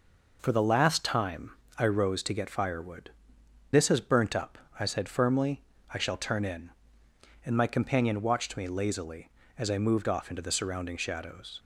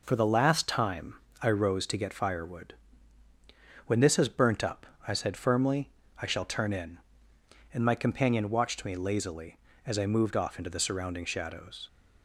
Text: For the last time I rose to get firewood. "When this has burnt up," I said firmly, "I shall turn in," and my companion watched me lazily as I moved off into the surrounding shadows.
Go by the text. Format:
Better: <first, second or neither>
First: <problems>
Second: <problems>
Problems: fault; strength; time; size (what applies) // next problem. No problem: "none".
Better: second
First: pauses between "time" and "I"; slight; at 1.5 s; 0.26 s long // skips "When"; at 3.4 s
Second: pauses between "time" and "I"; slight; at 1.1 s; 0.26 s long